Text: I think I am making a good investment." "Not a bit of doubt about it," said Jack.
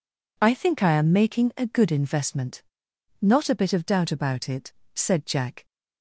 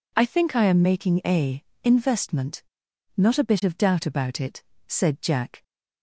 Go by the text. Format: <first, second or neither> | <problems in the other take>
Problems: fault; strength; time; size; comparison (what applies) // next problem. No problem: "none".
first | skips "good"; at 1.7 s